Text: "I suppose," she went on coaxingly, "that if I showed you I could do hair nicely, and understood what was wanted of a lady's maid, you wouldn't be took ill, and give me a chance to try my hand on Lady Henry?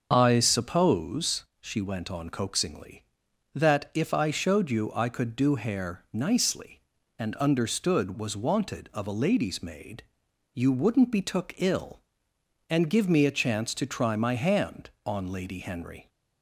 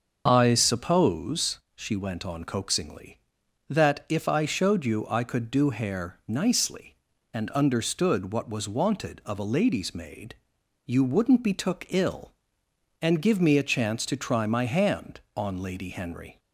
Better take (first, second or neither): second